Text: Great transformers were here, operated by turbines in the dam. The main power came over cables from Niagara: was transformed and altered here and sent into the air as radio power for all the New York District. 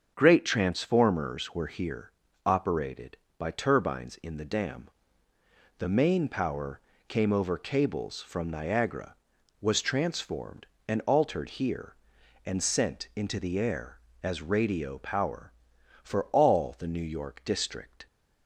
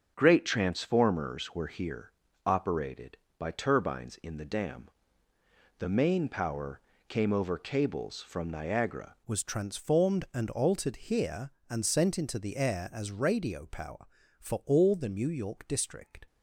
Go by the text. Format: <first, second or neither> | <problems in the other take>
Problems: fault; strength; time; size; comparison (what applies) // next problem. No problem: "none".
first | starts louder than the rest; until 1.1 s; 6.5 dB; also in the first // pauses between "power" and "came"; slight; at 6.8 s; 0.28 s long; slight in the first // changes voice at "was"; from 9.2 s on; 7.0 s long